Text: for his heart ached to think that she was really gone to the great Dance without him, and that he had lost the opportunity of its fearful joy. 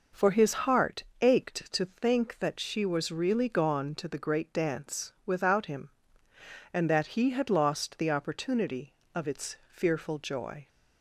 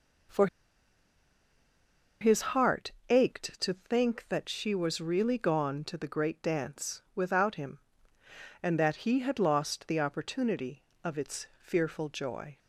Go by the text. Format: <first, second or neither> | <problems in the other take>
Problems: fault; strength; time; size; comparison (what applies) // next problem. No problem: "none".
first | pauses between "for" and "his"; strong; at 0.4 s; 1.7 s long // pauses between "heart" and "ached"; slight; at 2.9 s; 0.18 s long; slight in the first